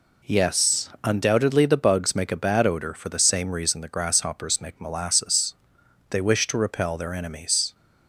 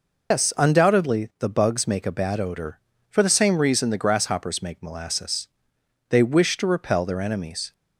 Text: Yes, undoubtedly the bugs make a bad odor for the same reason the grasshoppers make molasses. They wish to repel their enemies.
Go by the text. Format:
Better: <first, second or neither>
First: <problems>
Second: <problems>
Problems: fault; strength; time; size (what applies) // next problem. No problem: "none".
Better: first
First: none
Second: loses the start of "Yes"; at 0.3 s; 120 ms